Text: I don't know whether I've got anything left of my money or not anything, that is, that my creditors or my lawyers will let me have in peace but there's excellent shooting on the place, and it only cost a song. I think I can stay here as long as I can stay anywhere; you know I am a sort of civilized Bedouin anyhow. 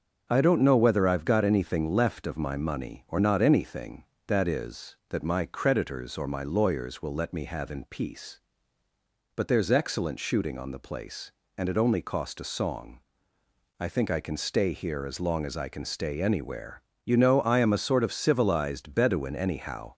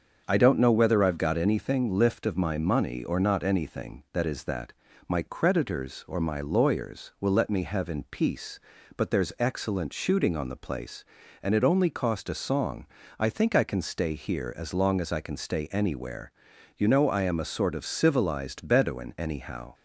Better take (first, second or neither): first